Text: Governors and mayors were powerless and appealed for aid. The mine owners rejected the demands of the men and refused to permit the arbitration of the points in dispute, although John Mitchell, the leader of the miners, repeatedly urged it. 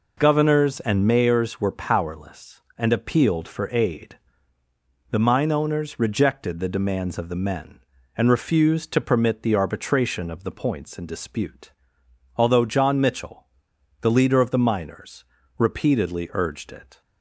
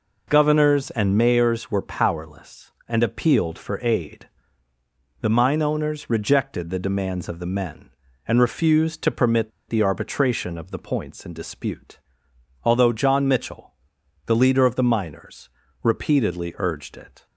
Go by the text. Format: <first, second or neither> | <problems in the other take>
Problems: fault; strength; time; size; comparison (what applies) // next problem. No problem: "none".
first | pauses between "permit" and "the"; slight; at 9.5 s; 0.18 s long